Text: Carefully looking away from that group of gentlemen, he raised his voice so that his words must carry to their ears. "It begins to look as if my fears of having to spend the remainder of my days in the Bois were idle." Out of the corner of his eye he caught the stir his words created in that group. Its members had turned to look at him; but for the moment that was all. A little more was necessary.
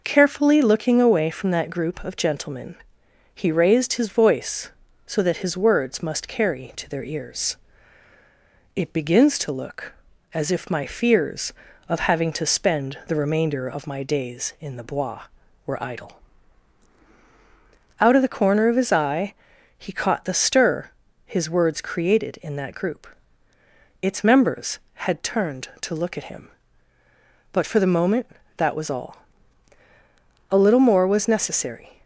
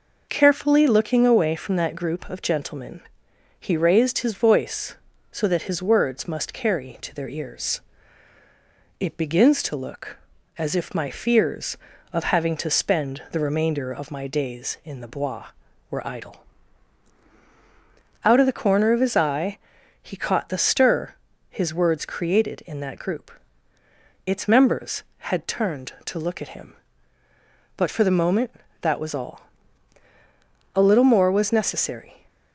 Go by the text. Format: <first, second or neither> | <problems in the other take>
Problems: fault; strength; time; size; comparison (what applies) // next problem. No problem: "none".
neither | pauses between "eye" and "he"; the same in both // pauses between "stir" and "his"; slight; the same in both